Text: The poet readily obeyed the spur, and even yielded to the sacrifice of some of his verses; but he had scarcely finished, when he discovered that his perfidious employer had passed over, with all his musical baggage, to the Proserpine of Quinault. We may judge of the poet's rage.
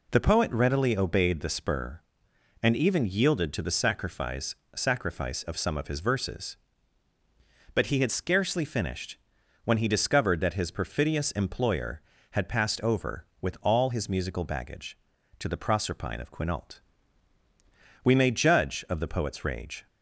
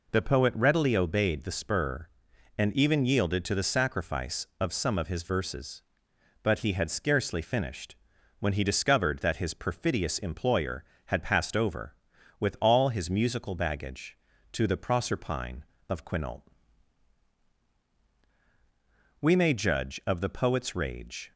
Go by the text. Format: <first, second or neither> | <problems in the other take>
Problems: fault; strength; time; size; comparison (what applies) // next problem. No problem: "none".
second | says "sacrifice" twice; at 4.7 s